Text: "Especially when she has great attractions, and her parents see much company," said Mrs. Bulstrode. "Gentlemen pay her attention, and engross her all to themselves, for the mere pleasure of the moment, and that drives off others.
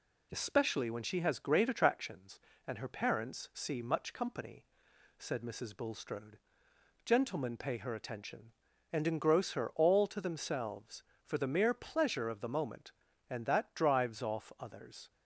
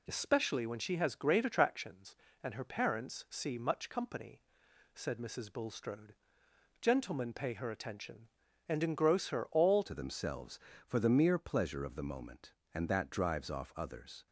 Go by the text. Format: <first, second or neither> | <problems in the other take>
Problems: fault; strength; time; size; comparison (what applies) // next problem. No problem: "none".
first | changes voice at "to"; from 9.8 s on; 4.4 s long